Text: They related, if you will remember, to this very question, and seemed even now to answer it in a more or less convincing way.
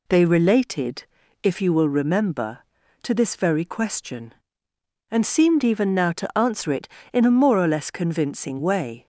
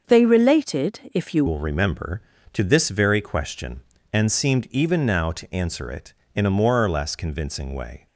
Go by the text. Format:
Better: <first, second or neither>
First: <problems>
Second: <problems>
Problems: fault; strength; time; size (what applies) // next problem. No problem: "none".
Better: first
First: none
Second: starts louder than the rest; until 1.0 s; 6.5 dB // changes voice at "will"; from 1.4 s on; 6.6 s long